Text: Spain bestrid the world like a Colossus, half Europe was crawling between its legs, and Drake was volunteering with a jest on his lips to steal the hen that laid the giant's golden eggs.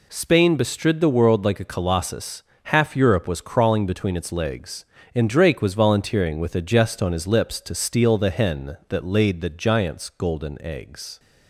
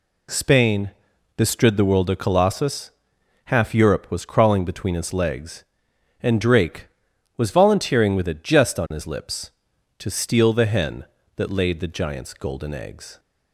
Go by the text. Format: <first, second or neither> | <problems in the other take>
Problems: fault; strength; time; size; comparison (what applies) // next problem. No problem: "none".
first | pauses between "Spain" and "bestrid"; noticeable; at 0.9 s; 0.46 s long // skips "like"; at 2.0 s